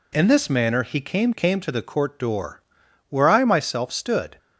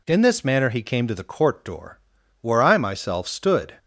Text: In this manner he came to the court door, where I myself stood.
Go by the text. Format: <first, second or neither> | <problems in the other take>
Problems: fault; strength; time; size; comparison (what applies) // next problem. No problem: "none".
second | says "came" twice; at 1.3 s